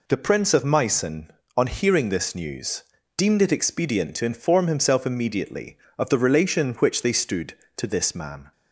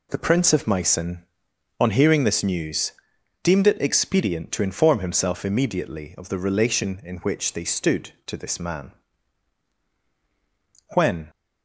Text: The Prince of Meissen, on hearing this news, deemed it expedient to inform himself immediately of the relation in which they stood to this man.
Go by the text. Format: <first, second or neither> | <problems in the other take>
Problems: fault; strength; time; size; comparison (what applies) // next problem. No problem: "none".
first | goes on to say "When"; slight; from 10.9 s on; 0.34 s long